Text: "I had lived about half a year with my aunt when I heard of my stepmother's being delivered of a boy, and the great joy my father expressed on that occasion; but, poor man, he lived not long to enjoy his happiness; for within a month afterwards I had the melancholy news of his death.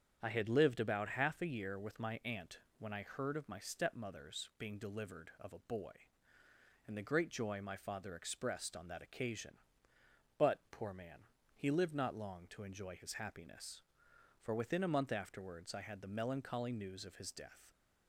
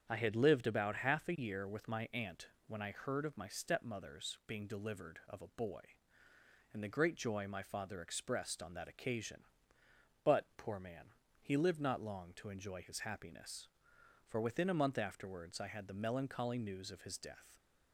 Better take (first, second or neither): neither